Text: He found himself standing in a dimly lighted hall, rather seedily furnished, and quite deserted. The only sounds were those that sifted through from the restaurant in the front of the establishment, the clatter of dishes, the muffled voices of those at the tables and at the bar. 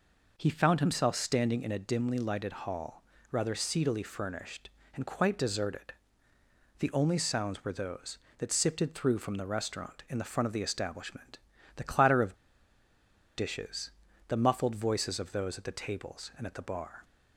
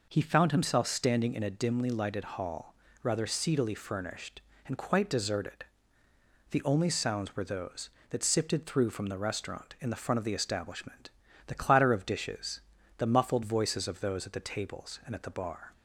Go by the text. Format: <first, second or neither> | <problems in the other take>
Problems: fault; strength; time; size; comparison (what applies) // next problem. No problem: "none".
second | pauses between "of" and "dishes"; at 12.3 s; 1.0 s long